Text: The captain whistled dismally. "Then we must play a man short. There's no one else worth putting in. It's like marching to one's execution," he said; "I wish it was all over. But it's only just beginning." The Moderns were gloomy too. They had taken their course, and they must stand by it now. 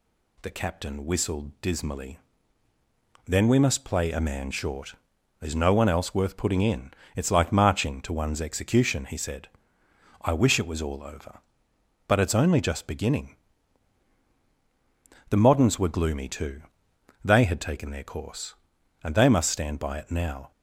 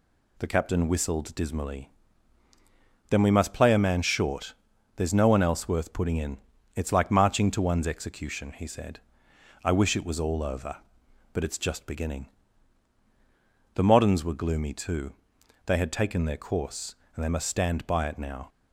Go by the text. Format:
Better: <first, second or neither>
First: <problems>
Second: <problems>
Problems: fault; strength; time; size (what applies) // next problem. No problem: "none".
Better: first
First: none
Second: skips "only"; at 11.5 s